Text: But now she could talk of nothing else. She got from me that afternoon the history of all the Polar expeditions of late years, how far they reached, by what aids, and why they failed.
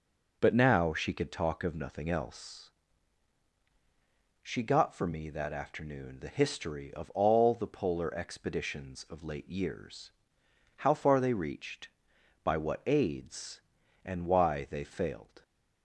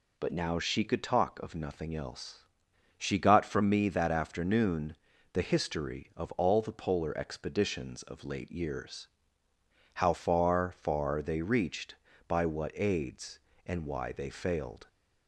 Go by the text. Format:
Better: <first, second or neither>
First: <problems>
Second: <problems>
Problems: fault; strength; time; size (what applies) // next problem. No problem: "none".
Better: first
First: none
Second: pauses between "afternoon" and "the"; at 4.9 s; 0.38 s long // says "far" twice; at 10.7 s